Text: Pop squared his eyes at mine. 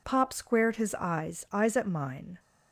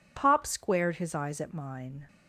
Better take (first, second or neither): second